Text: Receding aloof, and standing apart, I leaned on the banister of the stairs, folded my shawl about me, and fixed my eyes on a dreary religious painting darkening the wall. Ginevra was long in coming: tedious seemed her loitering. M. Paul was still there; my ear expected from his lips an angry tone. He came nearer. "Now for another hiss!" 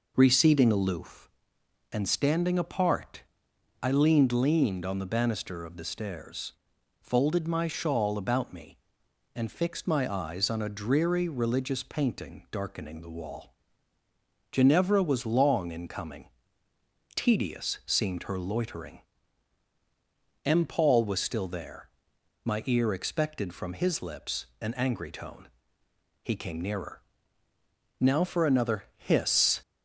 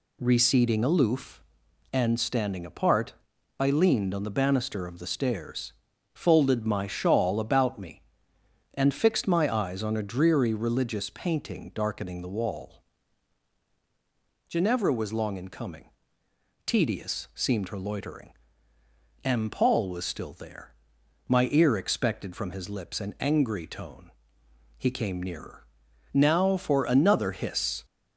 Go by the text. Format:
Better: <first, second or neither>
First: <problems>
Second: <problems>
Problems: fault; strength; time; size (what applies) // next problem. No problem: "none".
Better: second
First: says "leaned" twice; at 4.3 s // pauses between "lips" and "an"; slight; at 24.4 s; 0.16 s long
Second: none